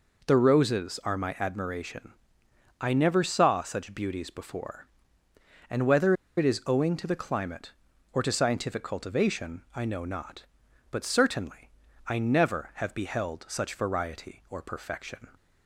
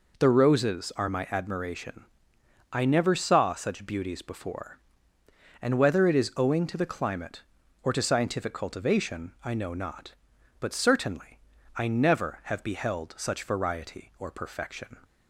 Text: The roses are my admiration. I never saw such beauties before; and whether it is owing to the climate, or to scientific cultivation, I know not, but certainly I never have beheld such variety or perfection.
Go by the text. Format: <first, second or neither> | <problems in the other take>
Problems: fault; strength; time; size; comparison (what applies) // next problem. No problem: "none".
second | pauses between "whether" and "it"; slight; at 6.1 s; 0.22 s long // pauses between "certainly" and "I"; slight; at 11.7 s; 0.36 s long; slight in the second